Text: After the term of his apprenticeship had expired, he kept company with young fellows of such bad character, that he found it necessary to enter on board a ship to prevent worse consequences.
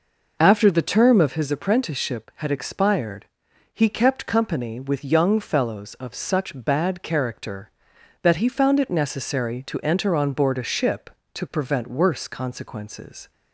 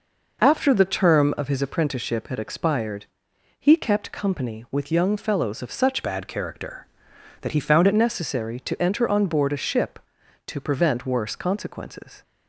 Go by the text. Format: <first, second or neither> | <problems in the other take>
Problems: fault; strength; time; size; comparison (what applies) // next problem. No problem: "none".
first | changes voice from "bad" to "it"; from 6.0 to 7.9 s; 1.9 s long